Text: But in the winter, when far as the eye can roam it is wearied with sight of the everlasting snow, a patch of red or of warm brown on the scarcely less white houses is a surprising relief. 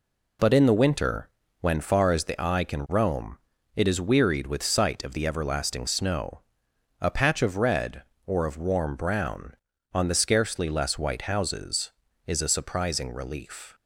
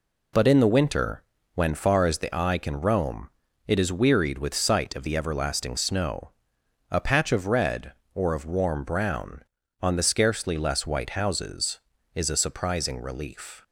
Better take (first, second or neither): neither